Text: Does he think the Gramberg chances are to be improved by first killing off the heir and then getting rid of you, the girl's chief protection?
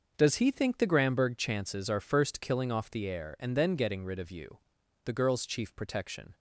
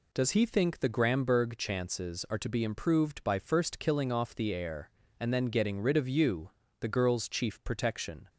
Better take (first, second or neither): second